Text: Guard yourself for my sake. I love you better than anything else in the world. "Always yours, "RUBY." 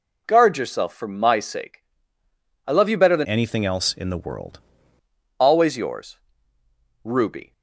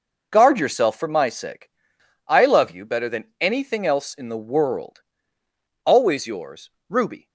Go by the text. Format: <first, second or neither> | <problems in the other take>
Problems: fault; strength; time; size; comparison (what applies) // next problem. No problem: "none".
second | changes voice from "anything" to "world"; from 3.2 to 4.5 s; 1.3 s long